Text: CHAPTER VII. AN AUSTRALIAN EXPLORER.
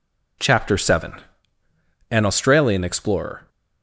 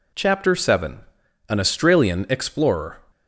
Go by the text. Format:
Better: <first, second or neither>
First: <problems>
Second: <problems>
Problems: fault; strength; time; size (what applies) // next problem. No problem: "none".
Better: neither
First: none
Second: none